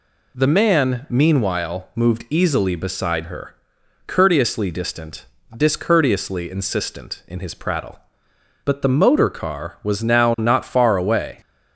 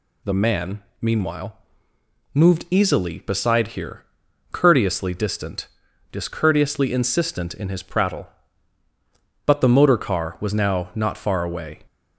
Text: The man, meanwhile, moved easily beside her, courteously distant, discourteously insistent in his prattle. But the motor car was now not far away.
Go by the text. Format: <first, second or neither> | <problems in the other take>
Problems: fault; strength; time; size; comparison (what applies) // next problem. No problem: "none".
first | says "here" for "her"; at 3.6 s